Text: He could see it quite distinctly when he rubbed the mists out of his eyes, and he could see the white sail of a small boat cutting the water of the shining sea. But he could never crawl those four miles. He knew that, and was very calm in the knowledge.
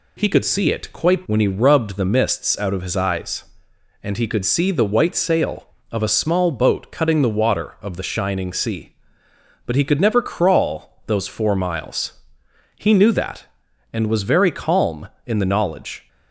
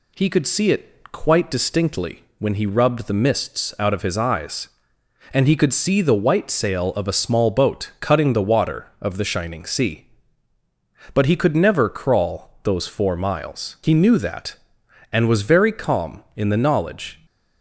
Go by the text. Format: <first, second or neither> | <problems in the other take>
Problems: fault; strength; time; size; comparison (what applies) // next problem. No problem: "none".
second | skips "distinctly"; at 1.2 s